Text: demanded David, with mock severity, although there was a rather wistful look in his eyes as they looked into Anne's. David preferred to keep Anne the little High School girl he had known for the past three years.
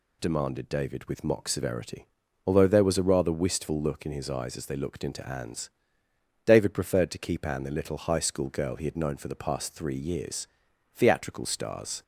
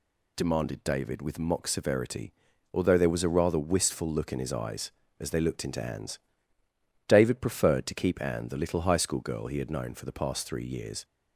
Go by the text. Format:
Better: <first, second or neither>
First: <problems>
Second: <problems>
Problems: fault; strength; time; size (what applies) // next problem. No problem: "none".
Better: second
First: goes on to say "Theatrical stars"; noticeable; from 10.9 s on; 1.0 s long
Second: none